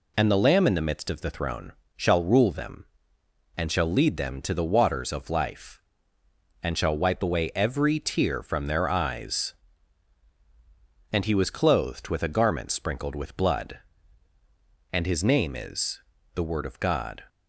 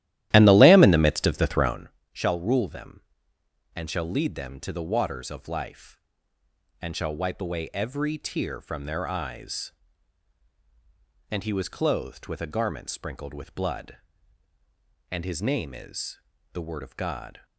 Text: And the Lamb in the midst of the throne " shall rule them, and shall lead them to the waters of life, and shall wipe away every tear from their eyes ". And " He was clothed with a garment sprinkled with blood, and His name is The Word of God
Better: first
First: pauses between "is" and "The"; slight; at 16.0 s; 0.32 s long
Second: starts louder than the rest; strong; until 1.9 s; 14 dB // pauses between "is" and "The"; slight; at 16.2 s; 0.32 s long

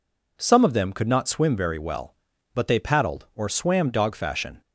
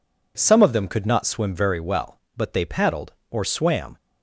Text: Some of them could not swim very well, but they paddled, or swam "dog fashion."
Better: first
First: none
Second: stops before "dog fashion"; at 3.9 s

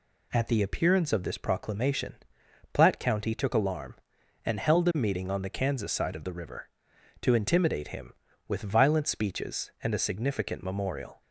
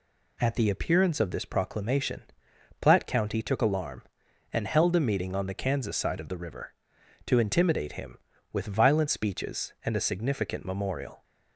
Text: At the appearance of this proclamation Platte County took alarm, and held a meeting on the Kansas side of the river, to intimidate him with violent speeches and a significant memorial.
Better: neither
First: pauses between "proclamation" and "Platte"; noticeable; at 2.1 s; 0.56 s long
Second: pauses between "proclamation" and "Platte"; noticeable; at 2.2 s; 0.56 s long

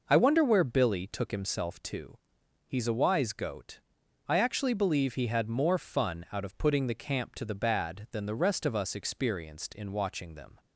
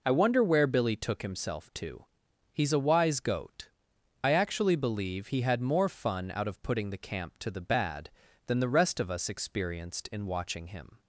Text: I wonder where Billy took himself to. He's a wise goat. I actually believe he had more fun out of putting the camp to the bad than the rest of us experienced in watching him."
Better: second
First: says "them" for "him"; at 10.3 s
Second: none

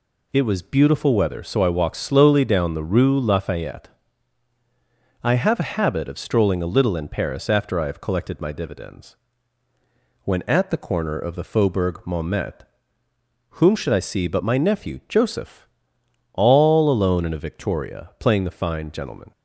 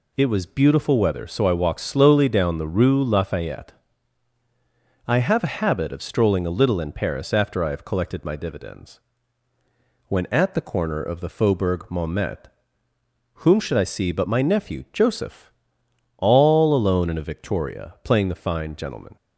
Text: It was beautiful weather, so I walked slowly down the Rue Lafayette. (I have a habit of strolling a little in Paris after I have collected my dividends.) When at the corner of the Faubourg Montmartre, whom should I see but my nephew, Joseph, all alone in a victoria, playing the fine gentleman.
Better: neither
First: none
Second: none

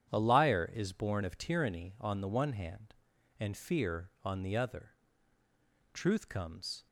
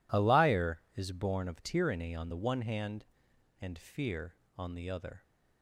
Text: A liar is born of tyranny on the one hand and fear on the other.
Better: second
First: starts louder than the rest; strong; until 1.1 s; 9 dB // goes on to say "Truth comes"; noticeable; from 5.9 s on; 0.94 s long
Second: none

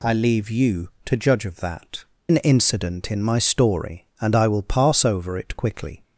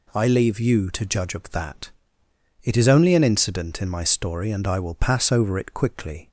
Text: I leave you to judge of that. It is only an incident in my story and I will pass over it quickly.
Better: second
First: skips "It is only"; at 2.1 s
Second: none

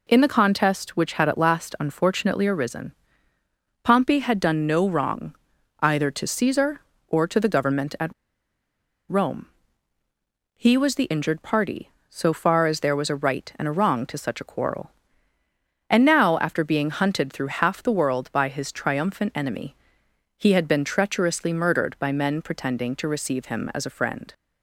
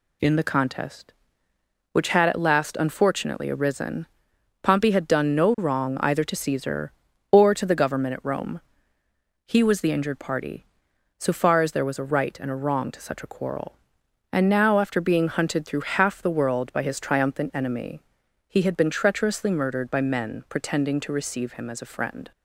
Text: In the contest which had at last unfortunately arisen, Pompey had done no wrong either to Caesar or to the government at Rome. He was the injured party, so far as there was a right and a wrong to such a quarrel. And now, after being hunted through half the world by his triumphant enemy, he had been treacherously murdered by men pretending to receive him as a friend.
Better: second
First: pauses between "wrong" and "either"; noticeable; at 5.3 s; 0.46 s long // pauses between "at" and "Rome"; noticeable; at 8.1 s; 0.95 s long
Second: none

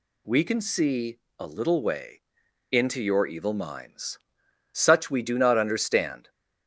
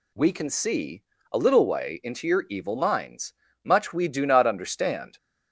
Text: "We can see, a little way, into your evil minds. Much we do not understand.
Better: second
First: says "Such" for "Much"; at 4.7 s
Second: none

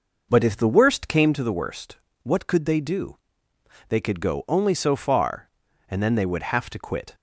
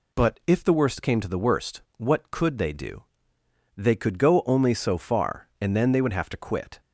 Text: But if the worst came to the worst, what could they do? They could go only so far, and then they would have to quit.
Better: second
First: starts louder than the rest; noticeable; until 1.3 s; 5.5 dB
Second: none

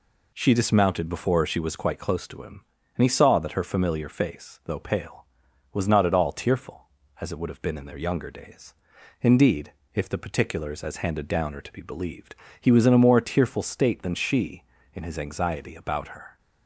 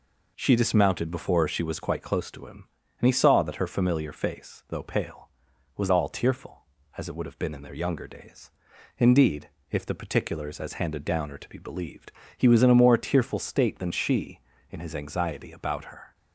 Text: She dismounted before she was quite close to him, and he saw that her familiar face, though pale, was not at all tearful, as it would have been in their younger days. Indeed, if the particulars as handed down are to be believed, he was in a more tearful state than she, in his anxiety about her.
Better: first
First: none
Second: skips "not at"; at 5.9 s

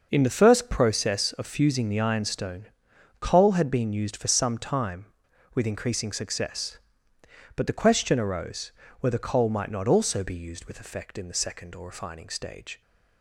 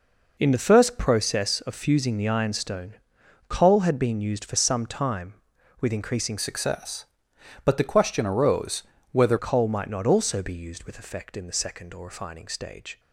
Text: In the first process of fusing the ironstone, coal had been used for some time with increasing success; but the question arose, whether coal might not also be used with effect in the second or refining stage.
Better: first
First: none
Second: changes voice from "success" to "whether"; from 6.3 to 9.3 s; 3.0 s long

